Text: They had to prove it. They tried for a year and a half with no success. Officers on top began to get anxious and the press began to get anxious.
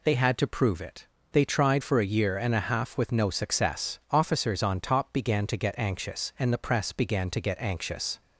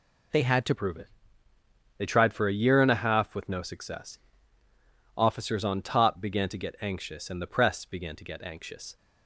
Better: first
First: none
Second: changes voice at "prove"; from 0.7 s on; 8.2 s long

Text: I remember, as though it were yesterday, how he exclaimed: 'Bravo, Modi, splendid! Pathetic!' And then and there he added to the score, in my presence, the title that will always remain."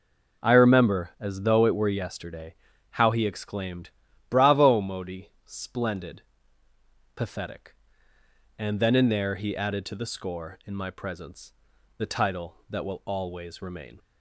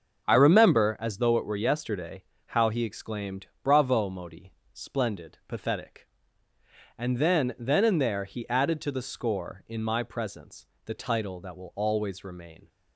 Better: first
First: none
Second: starts louder than the rest; until 1.3 s; 6.5 dB // says "then" twice; at 7.5 s

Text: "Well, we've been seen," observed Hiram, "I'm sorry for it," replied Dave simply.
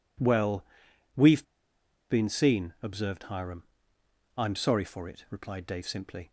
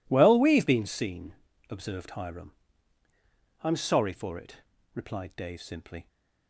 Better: second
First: pauses between "we've" and "been"; noticeable; at 1.4 s; 0.65 s long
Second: none

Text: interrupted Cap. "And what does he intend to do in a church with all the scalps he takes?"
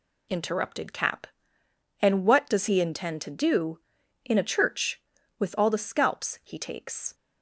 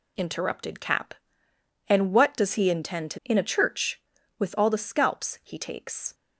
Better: first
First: none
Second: skips "do"; at 3.2 s

